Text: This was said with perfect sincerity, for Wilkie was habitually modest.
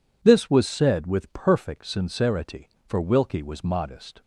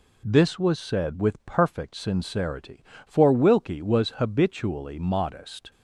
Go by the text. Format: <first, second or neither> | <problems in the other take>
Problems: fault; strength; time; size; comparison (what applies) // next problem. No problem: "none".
second | skips "habitually"; at 3.6 s